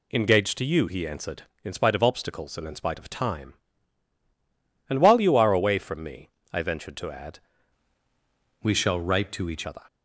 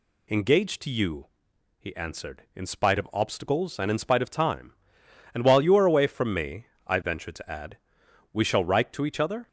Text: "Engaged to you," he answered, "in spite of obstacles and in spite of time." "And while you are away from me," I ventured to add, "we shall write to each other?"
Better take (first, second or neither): second